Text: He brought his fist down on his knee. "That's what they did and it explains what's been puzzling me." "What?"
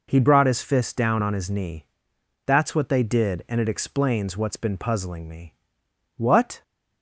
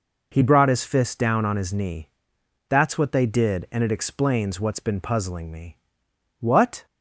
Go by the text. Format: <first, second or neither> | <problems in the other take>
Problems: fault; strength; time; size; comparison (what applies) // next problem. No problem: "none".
neither | none